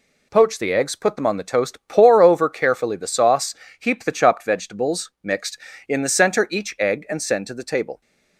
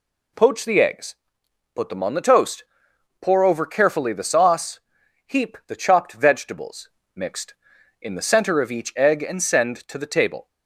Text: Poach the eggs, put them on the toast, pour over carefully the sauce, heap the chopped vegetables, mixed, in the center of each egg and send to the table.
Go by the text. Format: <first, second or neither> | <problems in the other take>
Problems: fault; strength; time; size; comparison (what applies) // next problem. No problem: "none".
second | skips "of"; at 6.4 s